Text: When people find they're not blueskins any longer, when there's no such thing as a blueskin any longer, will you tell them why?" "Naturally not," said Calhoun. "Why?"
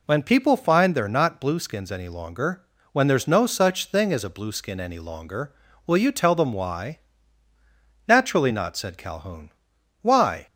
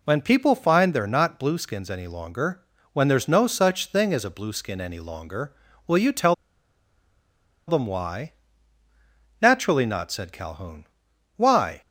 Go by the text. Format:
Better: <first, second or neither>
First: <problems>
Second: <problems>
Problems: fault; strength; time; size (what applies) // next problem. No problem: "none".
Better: first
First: none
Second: pauses between "tell" and "them"; strong; at 6.3 s; 1.3 s long